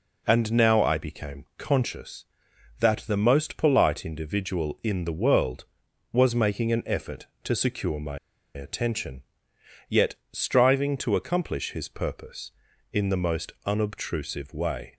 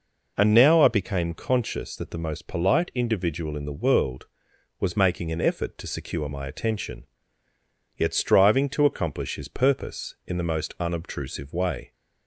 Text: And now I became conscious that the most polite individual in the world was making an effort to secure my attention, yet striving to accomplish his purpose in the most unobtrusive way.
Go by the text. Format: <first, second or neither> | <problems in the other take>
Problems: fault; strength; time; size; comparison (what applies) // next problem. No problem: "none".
second | pauses between "my" and "attention"; at 8.1 s; 0.37 s long // pauses between "yet" and "striving"; slight; at 10.1 s; 0.16 s long